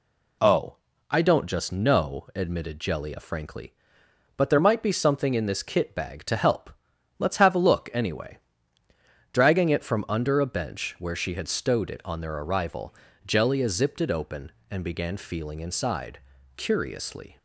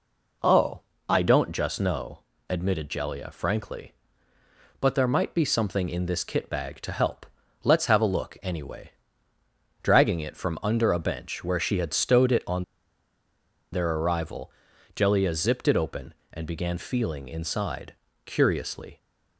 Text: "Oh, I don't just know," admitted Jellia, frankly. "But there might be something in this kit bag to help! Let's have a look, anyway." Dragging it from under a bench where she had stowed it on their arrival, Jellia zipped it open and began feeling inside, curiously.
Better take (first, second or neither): first